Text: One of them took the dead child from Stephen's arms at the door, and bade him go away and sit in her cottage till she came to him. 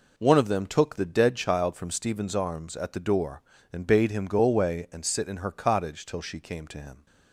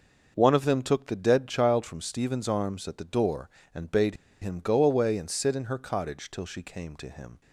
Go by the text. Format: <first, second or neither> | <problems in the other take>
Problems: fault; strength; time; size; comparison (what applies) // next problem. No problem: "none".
first | starts louder than the rest; until 1.3 s; 6 dB // pauses between "bade" and "him"; slight; at 4.1 s; 0.26 s long